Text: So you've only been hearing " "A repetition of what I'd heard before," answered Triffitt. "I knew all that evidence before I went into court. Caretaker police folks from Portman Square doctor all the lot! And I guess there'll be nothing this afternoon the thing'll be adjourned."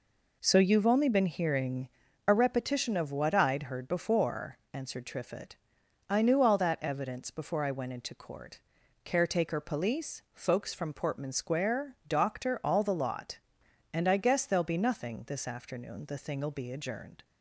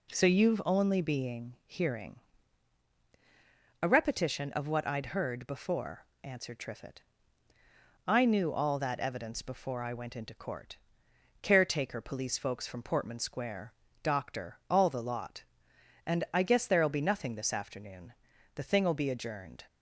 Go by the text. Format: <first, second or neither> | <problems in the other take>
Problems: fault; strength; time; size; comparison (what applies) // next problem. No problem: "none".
first | says "being" for "been"; at 1.0 s // pauses between "Square" and "doctor"; slight; at 13.7 s; 0.28 s long // pauses between "afternoon" and "the"; at 18.1 s; 0.40 s long